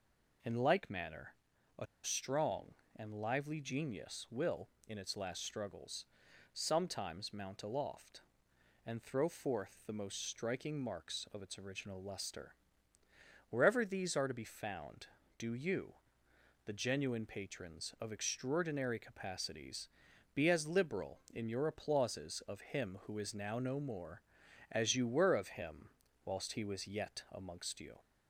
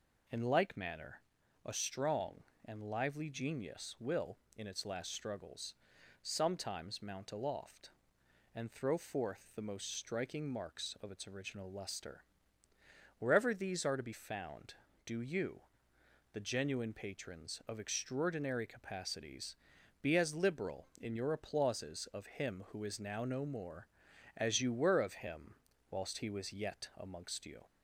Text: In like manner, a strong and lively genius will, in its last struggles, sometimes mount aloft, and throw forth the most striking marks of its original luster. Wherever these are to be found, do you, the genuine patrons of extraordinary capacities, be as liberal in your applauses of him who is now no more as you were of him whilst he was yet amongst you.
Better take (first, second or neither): second